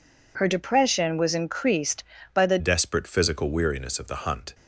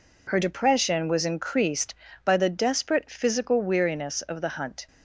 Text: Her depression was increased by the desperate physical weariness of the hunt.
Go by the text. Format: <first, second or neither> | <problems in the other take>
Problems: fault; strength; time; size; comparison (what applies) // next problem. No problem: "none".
second | changes voice at "desperate"; from 2.5 s on; 2.0 s long